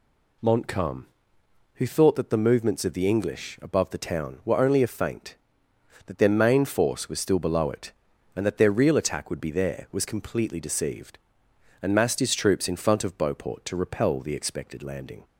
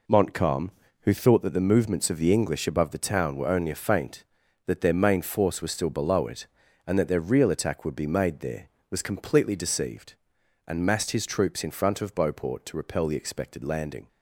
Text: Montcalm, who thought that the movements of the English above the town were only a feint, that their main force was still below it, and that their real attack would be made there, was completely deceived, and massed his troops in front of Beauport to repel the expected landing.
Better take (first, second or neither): second